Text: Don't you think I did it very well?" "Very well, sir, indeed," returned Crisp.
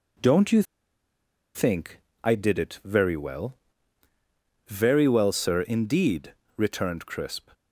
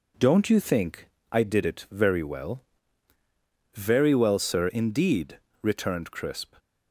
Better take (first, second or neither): second